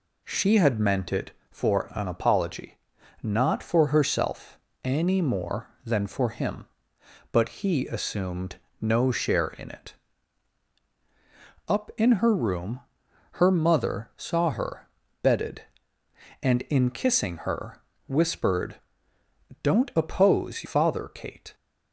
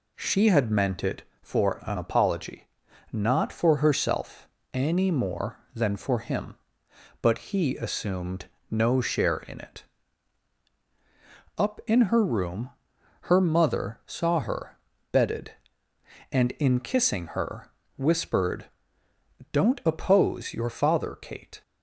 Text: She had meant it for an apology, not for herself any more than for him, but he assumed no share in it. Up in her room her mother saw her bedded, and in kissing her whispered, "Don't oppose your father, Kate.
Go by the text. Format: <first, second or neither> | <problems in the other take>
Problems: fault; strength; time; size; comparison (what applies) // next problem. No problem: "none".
second | pauses between "herself" and "any"; slight; at 4.5 s; 0.24 s long; slight in the second // pauses between "assumed" and "no"; slight; at 8.5 s; 0.24 s long; slight in the second // pauses between "room" and "her"; noticeable; at 12.8 s; 0.52 s long; noticeable in the second // pauses between "her" and "bedded"; slight; at 14.8 s; 0.36 s long; slight in the second // pauses between "her" and "whispered"; slight; at 17.8 s; 0.26 s long; slight in the second // skips "your"; at 20.6 s